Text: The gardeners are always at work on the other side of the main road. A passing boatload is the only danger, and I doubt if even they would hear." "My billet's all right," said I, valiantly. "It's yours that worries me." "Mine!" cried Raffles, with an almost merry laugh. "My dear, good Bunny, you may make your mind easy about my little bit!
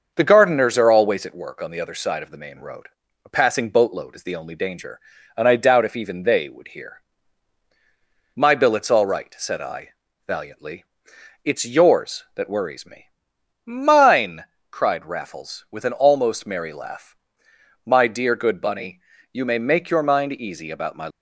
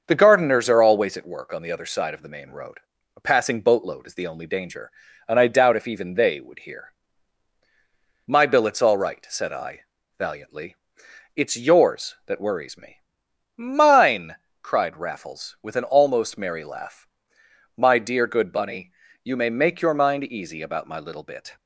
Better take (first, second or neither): second